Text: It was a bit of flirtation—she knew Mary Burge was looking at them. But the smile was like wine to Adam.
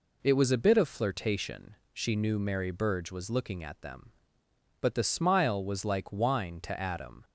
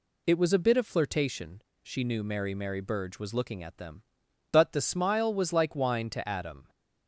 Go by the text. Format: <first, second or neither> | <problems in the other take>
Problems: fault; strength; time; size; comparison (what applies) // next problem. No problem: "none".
first | says "Mary" twice; at 2.5 s